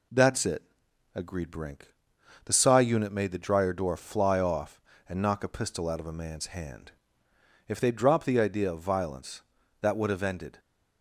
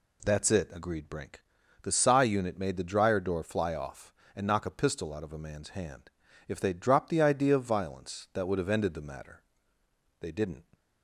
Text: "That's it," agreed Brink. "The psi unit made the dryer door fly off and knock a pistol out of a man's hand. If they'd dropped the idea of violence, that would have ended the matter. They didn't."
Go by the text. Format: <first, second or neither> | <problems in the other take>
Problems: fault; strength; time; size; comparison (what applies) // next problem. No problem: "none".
second | stops before "the matter They didn't"; at 10.5 s